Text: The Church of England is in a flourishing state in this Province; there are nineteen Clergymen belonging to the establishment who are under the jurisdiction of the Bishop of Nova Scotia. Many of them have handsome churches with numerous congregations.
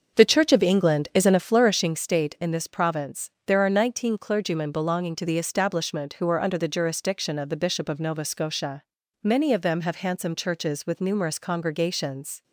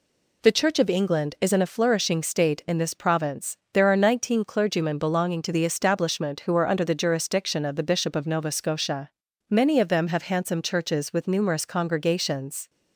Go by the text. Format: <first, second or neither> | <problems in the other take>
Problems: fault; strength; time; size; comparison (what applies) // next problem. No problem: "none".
second | starts louder than the rest; until 2.0 s; 6.5 dB